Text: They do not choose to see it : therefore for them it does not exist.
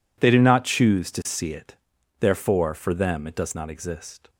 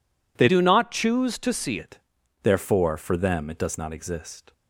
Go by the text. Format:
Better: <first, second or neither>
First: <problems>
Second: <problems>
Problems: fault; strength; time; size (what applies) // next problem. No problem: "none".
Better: first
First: none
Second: changes voice from "do" to "see"; from 0.4 to 1.7 s; 1.3 s long